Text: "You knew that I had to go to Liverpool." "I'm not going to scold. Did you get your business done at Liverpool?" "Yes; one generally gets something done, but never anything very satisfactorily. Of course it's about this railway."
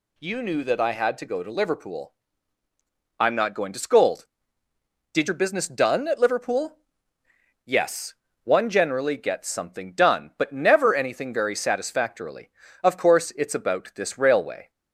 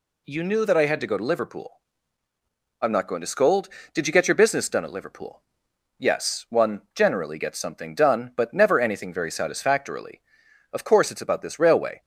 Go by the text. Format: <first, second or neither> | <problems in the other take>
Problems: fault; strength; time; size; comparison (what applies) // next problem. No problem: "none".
second | skips "you get"; at 5.2 s